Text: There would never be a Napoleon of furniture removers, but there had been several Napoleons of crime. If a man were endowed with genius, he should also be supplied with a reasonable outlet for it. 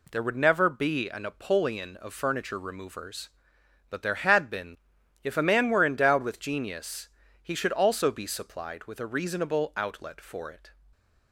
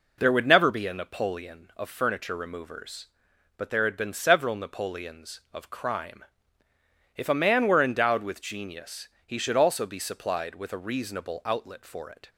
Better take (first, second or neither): second